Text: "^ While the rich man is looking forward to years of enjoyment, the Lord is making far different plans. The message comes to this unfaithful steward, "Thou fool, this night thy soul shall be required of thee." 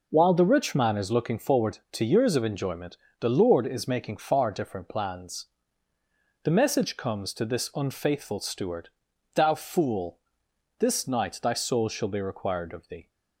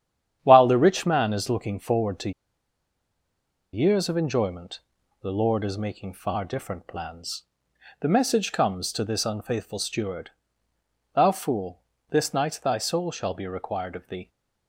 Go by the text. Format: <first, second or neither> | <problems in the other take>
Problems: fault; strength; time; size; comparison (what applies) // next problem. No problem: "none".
first | starts louder than the rest; strong; until 1.4 s; 9.5 dB // pauses between "to" and "years"; strong; at 2.3 s; 1.4 s long